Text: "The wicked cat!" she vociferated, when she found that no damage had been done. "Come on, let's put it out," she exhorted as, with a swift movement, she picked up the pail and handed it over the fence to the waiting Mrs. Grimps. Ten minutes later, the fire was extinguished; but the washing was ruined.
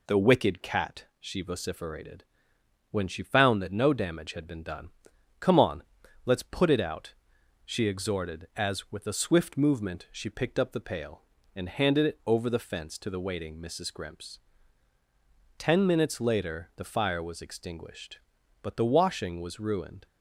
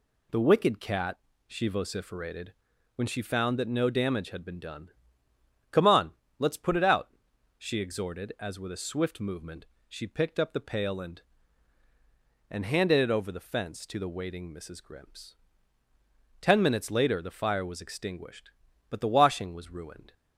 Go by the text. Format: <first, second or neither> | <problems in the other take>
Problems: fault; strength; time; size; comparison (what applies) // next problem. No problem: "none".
first | says "and" twice; at 12.4 s